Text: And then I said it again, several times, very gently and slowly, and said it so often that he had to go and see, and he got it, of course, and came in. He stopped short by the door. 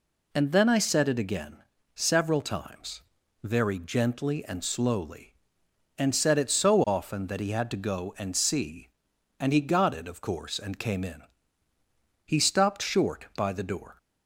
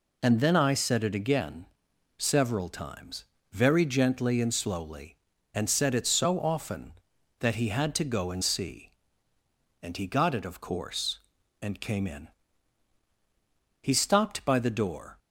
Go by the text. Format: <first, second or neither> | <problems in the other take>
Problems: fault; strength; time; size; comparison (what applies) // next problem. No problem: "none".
first | skips "short"; at 14.4 s